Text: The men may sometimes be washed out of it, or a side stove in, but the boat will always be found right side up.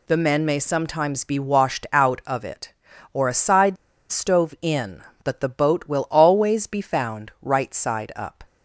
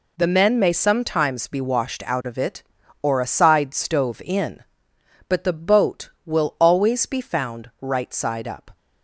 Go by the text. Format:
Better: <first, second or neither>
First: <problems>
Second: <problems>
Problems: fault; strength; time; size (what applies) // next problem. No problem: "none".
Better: second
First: pauses between "side" and "stove"; slight; at 3.7 s; 0.35 s long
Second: none